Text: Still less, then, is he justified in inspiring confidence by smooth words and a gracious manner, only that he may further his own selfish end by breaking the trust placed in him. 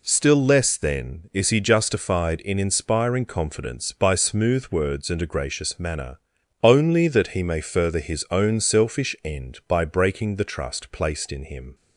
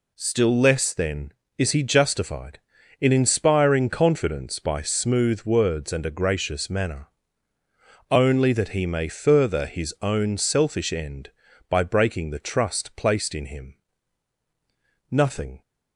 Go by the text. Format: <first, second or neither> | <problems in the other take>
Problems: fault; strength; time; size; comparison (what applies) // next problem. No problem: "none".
first | goes on to say "Nothing"; from 15.0 s on; 0.52 s long